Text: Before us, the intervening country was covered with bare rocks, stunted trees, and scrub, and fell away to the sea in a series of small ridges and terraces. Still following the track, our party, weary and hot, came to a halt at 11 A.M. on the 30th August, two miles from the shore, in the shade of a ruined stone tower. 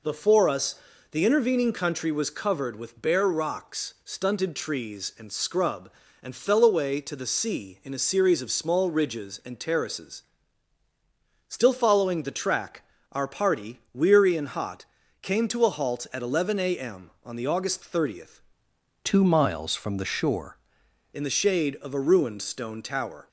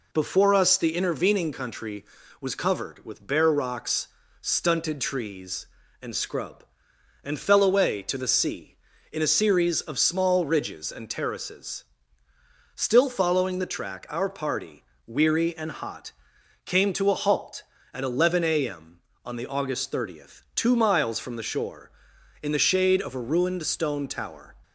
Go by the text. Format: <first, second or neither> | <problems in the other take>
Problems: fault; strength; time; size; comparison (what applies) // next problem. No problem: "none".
second | changes voice from "two" to "shore"; from 19.0 to 20.5 s; 1.5 s long